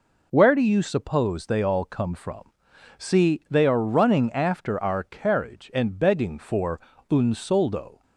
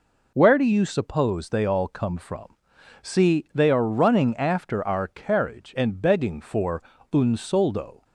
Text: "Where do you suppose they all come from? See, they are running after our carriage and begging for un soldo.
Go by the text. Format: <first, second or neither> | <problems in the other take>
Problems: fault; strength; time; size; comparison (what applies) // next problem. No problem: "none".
neither | pauses between "for" and "un"; slight; the same in both